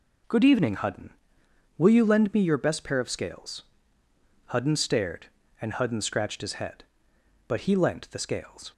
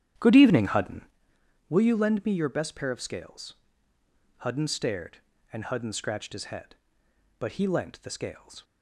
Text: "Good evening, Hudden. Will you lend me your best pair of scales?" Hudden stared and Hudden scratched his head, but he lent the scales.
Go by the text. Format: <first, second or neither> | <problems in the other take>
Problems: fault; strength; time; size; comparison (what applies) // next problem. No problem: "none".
first | starts louder than the rest; strong; until 1.2 s; 10.5 dB